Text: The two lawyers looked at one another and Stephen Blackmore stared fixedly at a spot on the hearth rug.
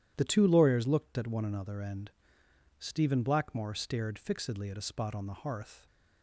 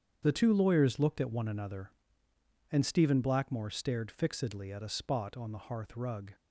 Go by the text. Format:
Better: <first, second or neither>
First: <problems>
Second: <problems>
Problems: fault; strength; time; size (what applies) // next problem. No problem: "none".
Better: second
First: starts louder than the rest; strong; until 1.1 s; 11 dB // pauses between "and" and "Stephen"; noticeable; at 2.0 s; 0.68 s long // stops before "rug"; at 5.8 s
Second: starts louder than the rest; strong; until 1.2 s; 8 dB